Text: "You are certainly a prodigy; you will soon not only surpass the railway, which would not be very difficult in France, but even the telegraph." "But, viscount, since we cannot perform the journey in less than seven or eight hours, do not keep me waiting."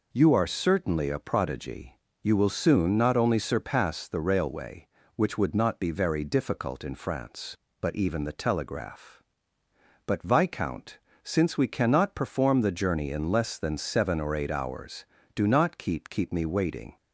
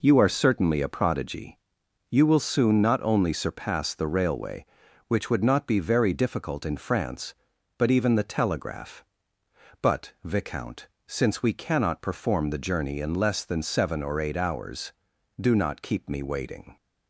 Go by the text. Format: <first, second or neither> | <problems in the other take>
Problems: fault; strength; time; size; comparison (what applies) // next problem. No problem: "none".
second | says "keep" twice; at 16.0 s